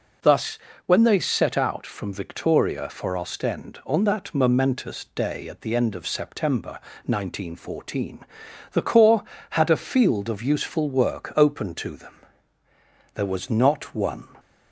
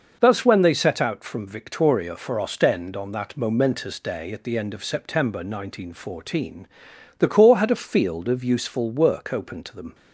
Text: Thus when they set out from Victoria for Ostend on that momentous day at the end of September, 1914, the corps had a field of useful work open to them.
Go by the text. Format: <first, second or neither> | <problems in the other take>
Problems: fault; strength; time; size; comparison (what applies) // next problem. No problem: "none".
second | pauses between "Thus" and "when"; slight; at 0.5 s; 0.28 s long // goes on to say "There was not one"; noticeable; from 13.1 s on; 1.1 s long